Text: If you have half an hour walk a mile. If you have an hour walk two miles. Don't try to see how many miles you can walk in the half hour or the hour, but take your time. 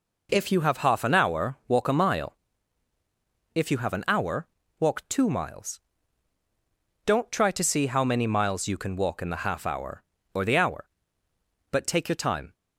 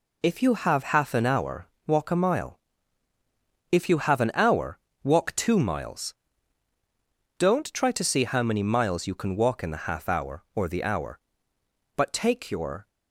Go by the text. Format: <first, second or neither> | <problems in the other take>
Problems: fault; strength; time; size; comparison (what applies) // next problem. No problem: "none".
first | pauses between "hour" and "walk"; slight; at 1.6 s; 0.18 s long // pauses between "hour" and "walk"; slight; at 4.7 s; 0.24 s long; slight in the first // stops before "time"; at 12.8 s